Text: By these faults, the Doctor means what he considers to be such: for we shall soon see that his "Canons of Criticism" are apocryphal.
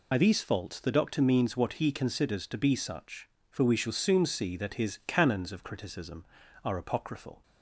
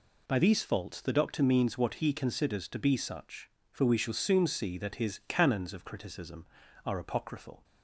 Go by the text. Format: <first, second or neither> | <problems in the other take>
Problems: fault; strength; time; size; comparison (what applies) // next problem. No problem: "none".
second | loses the start of "By"; at 0.1 s; 50 ms